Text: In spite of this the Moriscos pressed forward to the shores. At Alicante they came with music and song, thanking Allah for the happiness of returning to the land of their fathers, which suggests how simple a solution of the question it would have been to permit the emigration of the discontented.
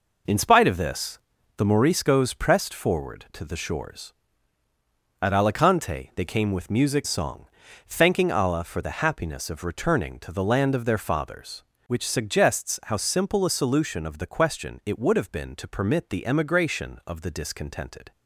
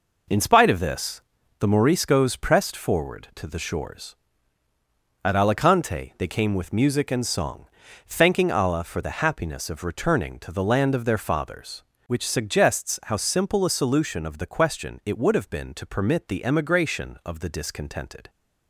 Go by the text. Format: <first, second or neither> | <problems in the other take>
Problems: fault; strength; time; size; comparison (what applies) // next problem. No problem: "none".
second | pauses between "this" and "the"; at 1.1 s; 0.38 s long; also in the second // skips "and"; at 7.0 s